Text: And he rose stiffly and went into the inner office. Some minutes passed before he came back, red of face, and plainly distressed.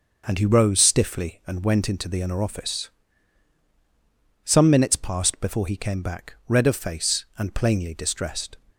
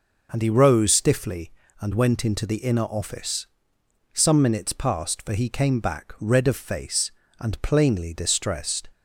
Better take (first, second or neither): first